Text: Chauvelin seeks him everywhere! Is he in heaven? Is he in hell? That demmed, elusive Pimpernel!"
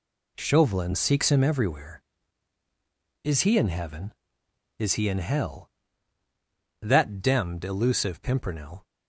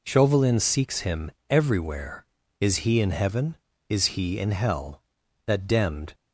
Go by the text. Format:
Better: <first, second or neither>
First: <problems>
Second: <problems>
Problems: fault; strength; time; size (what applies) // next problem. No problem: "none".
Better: first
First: none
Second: pauses between "him" and "everywhere"; slight; at 1.3 s; 0.18 s long // stops before "elusive Pimpernel"; at 6.1 s